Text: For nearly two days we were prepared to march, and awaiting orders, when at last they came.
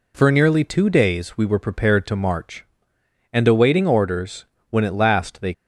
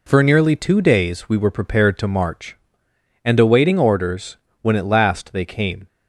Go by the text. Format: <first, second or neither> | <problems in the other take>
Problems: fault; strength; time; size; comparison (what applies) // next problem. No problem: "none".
second | stops before "came"; at 5.5 s